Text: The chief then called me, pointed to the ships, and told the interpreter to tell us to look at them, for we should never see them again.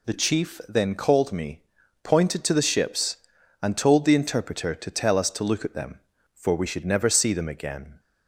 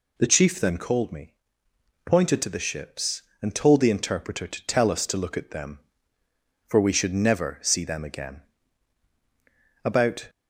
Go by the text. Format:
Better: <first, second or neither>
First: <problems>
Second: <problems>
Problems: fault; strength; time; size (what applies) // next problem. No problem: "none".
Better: first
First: none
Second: goes on to say "About"; slight; from 9.8 s on; 0.46 s long